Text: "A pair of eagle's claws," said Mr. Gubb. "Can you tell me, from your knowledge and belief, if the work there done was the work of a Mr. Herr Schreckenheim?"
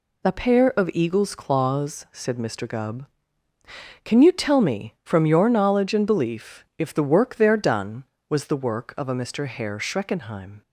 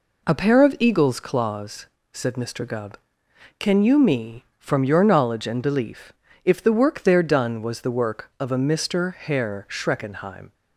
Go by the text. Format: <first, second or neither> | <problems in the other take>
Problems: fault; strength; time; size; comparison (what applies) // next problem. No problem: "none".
first | skips "tell"; at 3.9 s